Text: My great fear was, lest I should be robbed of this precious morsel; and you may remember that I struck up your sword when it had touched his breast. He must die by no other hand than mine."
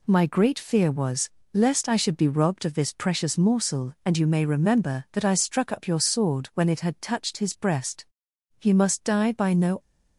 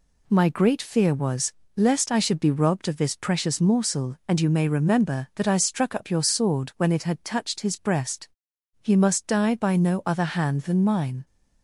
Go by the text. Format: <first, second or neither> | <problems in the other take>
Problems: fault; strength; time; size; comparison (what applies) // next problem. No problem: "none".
second | stops before "other hand than mine"; at 9.7 s